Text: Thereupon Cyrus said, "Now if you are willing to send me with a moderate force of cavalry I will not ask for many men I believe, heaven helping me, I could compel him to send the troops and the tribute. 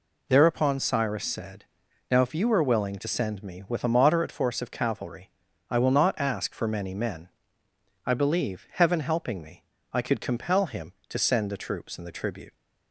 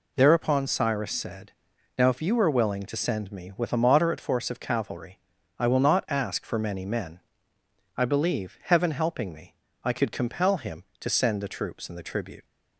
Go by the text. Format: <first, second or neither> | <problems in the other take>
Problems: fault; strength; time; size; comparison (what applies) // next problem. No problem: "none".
neither | pauses between "cavalry" and "I"; the same in both // pauses between "men" and "I"; noticeable; the same in both